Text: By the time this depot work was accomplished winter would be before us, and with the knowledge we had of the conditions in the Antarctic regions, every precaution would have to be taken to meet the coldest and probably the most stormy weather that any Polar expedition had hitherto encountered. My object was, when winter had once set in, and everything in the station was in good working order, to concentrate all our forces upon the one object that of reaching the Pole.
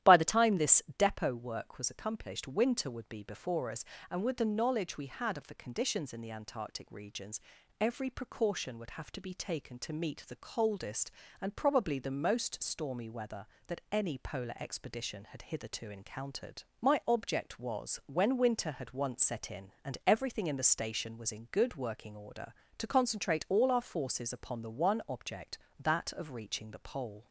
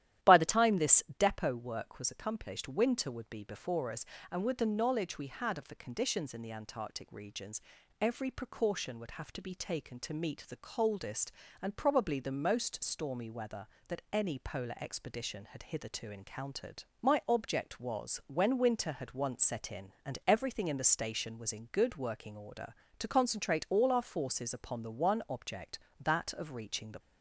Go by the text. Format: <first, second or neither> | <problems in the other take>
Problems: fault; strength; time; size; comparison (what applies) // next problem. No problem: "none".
first | starts louder than the rest; strong; until 1.3 s; 12 dB; strong in the first // stops before "Pole"; at 26.9 s